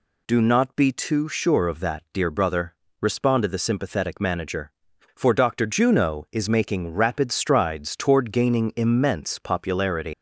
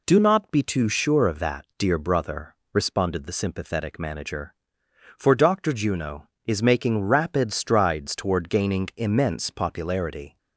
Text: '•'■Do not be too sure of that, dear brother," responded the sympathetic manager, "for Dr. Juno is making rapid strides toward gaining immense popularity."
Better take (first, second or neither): second